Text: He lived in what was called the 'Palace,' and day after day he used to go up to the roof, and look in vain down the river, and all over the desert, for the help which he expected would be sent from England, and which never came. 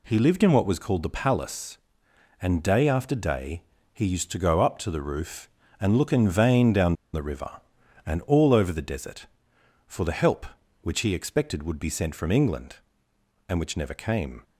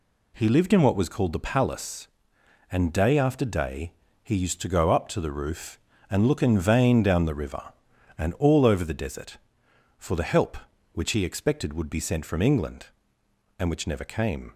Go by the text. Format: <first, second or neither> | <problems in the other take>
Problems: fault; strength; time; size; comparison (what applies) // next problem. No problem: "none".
second | pauses between "day" and "he"; slight; at 3.6 s; 0.28 s long; slight in the second // pauses between "down" and "the"; slight; at 6.9 s; 0.20 s long